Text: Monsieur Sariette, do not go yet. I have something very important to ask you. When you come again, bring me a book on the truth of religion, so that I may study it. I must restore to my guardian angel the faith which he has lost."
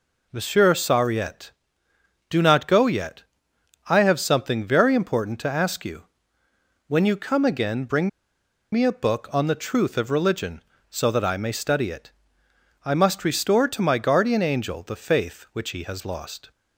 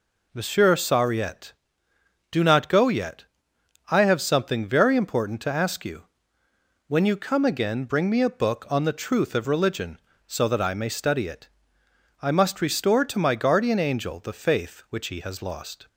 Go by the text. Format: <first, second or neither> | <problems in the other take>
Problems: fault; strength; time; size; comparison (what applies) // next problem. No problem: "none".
second | pauses between "bring" and "me"; noticeable; at 8.0 s; 0.62 s long